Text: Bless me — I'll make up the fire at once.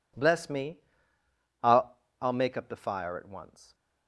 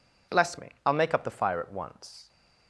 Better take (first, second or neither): second